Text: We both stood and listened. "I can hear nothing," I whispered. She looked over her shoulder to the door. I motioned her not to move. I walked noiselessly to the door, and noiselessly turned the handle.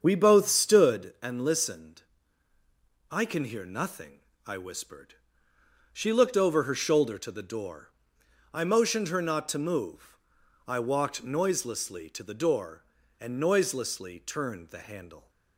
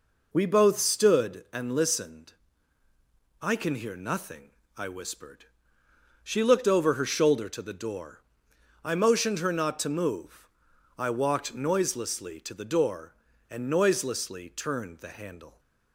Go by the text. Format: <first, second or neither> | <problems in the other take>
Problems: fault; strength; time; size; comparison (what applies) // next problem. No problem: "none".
second | starts louder than the rest; strong; until 1.1 s; 7.5 dB